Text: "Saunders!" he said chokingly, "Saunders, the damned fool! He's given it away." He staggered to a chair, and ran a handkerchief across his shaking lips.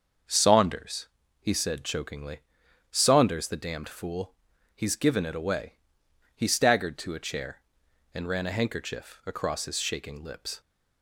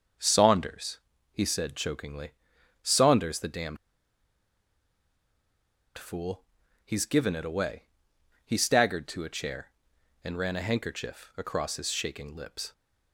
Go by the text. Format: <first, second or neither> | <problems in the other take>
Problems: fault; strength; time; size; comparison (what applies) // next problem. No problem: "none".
first | starts louder than the rest; until 1.5 s; 6.5 dB; also in the first // pauses between "damned" and "fool"; strong; at 3.7 s; 2.2 s long